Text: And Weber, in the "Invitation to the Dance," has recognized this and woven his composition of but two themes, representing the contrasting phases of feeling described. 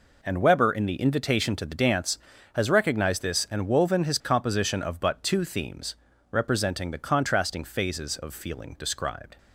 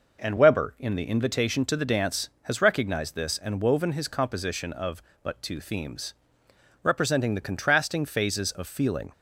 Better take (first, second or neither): first